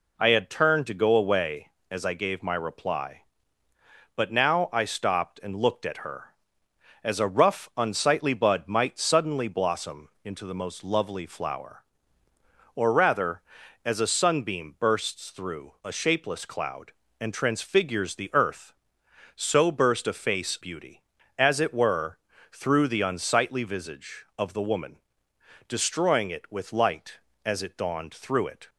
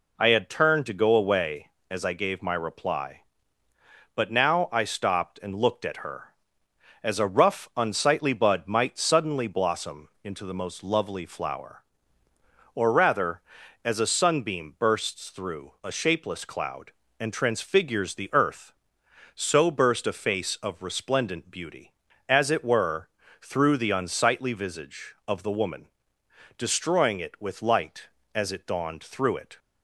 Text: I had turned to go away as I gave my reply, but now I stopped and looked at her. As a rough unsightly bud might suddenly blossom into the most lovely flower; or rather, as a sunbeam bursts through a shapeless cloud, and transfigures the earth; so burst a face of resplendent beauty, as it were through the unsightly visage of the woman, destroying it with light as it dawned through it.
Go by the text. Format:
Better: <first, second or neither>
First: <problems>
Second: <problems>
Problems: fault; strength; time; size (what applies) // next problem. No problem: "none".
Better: second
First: pauses between "blossom" and "into"; slight; at 10.0 s; 0.16 s long // skips "of resplendent"; at 20.5 s // pauses between "were" and "through"; slight; at 22.1 s; 0.34 s long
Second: pauses between "blossom" and "into"; slight; at 10.0 s; 0.16 s long // pauses between "were" and "through"; slight; at 23.0 s; 0.33 s long